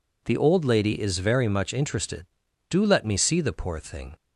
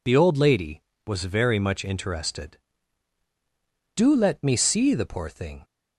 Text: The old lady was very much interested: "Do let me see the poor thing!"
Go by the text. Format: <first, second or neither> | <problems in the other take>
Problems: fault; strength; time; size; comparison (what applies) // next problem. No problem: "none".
second | says "is" for "was"; at 1.0 s